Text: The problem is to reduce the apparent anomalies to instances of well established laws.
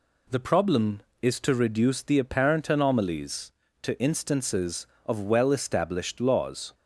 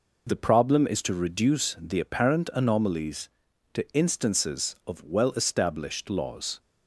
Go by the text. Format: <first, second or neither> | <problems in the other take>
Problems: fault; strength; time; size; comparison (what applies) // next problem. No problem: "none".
neither | none